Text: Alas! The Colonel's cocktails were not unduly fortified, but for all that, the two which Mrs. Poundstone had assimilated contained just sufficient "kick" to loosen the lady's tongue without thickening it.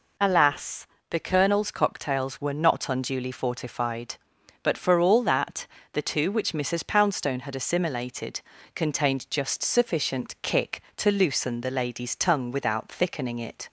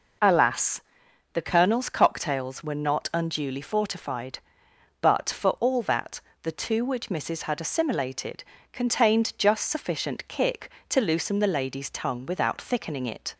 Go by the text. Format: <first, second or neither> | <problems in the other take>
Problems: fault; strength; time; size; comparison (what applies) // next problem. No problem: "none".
first | skips "Poundstone"; at 7.4 s // pauses between "assimilated" and "contained"; slight; at 8.4 s; 0.28 s long; slight in the first